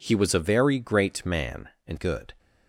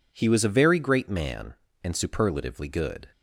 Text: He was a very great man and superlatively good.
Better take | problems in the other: second | skips "superlatively"; at 1.9 s

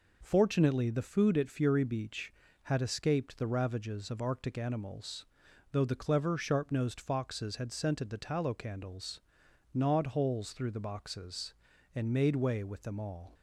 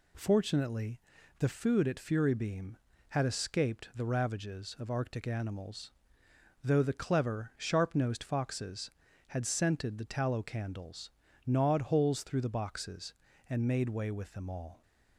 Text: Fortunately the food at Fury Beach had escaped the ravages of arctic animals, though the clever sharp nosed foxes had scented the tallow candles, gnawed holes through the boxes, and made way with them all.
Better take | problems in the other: first | pauses between "Fortunately" and "the"; at 0.9 s; 0.42 s long // says "Beam" for "Beach"; at 2.3 s

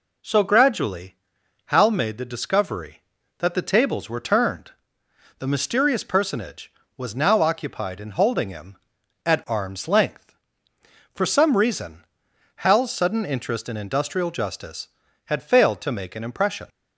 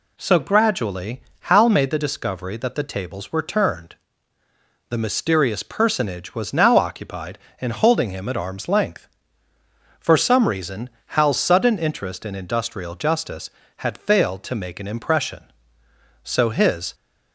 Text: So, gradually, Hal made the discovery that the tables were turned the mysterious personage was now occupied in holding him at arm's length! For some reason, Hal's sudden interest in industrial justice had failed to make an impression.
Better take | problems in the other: first | pauses between "turned" and "the"; noticeable; at 3.9 s; 0.94 s long; noticeable in the first // goes on to say "So his"; noticeable; from 16.2 s on; 0.70 s long

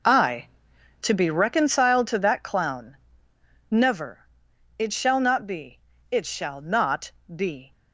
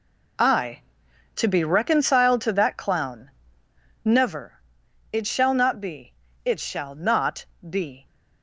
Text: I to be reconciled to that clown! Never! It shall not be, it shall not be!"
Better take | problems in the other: second | starts louder than the rest; noticeable; until 1.2 s; 5 dB // pauses between "not" and "be"; slight; at 7.1 s; 0.24 s long; slight in the second

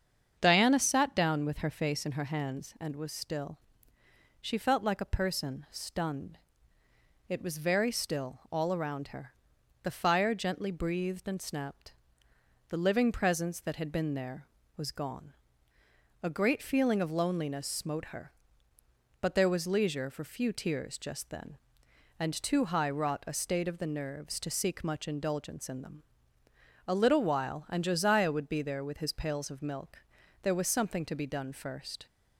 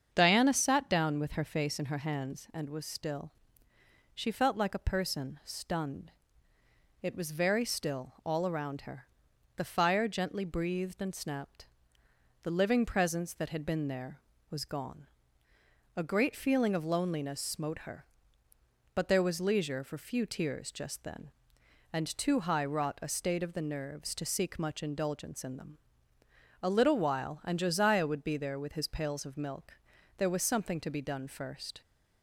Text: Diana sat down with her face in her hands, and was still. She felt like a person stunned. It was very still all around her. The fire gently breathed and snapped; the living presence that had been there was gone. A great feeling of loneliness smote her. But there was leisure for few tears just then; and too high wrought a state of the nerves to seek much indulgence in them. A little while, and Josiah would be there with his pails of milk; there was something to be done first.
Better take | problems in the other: neither | starts louder than the rest; strong; the same in both

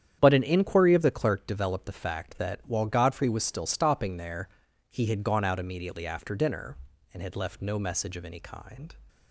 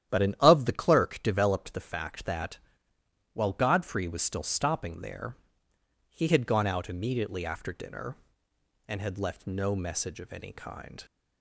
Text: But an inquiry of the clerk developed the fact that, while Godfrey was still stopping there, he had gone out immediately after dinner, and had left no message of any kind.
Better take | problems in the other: first | starts louder than the rest; strong; until 1.1 s; 10.5 dB; strong in the first // skips "inquiry"; at 0.3 s

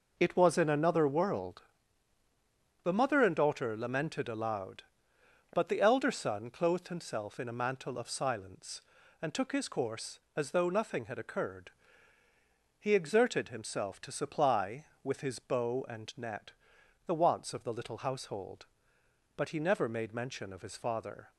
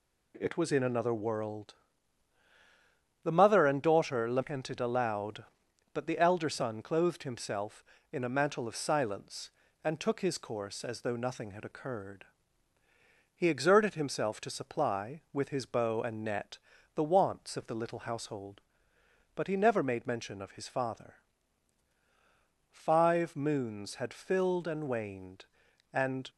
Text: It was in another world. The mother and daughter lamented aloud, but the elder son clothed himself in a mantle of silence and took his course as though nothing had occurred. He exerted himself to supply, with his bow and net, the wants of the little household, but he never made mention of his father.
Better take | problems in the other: first | goes on to say "Five moons had filled and waned and"; strong; from 22.7 s on; 3.5 s long

